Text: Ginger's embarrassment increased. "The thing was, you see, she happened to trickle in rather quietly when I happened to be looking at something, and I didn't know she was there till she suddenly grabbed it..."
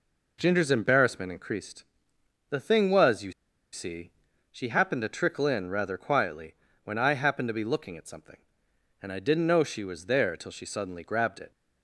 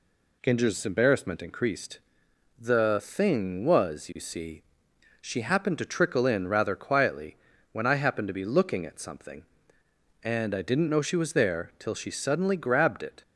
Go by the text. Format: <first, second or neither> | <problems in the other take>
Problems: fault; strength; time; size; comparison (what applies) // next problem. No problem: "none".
second | pauses between "you" and "see"; at 3.3 s; 0.39 s long // pauses between "quietly" and "when"; slight; at 6.5 s; 0.30 s long; slight in the second